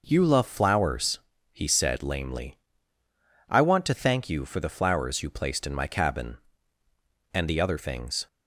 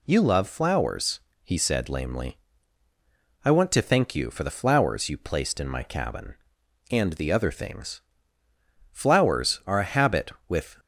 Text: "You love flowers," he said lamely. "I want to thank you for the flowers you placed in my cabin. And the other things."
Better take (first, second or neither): first